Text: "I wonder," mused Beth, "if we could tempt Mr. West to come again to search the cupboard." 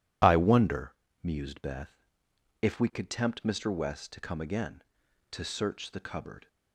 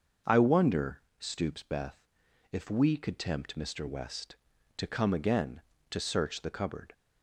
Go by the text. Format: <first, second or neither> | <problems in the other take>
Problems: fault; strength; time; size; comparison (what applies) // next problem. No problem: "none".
first | starts louder than the rest; noticeable; until 1.4 s; 6 dB // says "stoops" for "mused"; at 1.1 s